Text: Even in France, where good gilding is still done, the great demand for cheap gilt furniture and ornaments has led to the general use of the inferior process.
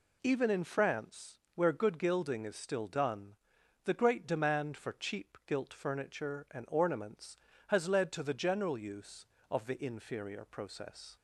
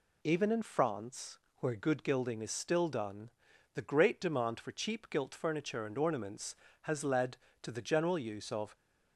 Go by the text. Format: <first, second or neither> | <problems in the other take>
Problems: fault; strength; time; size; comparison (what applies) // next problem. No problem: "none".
first | stops before "the inferior process"; at 8.7 s